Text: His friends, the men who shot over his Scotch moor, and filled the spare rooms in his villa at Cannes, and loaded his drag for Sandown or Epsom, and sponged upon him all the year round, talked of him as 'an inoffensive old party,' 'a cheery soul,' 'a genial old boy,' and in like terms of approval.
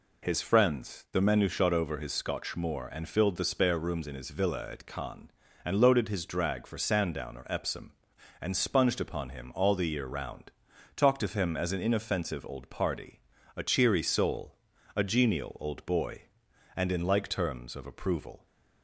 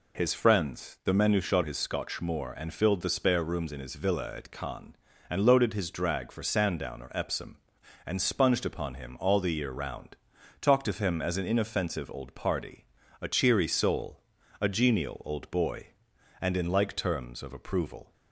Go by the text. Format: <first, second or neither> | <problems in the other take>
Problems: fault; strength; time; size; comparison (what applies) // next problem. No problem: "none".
first | skips "over"; at 1.6 s